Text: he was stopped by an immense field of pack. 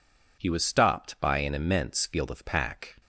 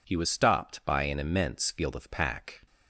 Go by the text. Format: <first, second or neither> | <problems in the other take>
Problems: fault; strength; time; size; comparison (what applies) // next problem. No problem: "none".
neither | none